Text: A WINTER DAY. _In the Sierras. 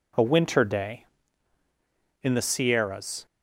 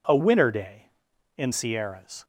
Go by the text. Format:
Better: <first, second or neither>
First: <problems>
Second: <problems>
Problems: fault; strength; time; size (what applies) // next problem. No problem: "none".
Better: first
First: none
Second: skips "the"; at 1.5 s